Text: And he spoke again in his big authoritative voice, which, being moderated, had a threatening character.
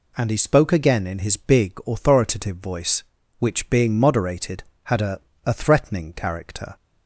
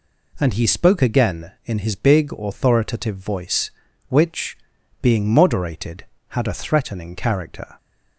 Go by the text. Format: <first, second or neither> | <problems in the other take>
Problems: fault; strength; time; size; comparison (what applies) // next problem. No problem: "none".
second | says "a" twice; at 5.4 s